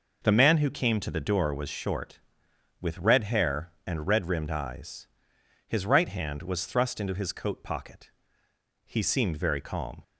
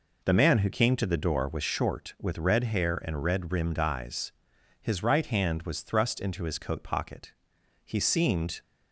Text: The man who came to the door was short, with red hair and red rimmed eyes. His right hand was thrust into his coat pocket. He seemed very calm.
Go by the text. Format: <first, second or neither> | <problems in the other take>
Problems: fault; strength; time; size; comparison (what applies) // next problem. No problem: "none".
first | stops before "very calm"; at 8.6 s